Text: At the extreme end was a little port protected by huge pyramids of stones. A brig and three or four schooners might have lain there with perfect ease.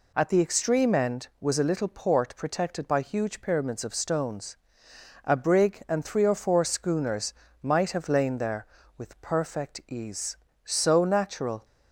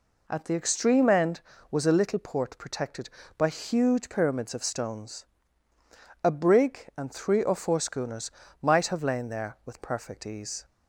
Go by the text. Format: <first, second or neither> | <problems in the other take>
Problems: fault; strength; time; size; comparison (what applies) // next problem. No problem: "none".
second | pauses between "schooners" and "might"; slight; at 7.3 s; 0.30 s long; slight in the second // goes on to say "So natural"; noticeable; from 10.6 s on; 1.0 s long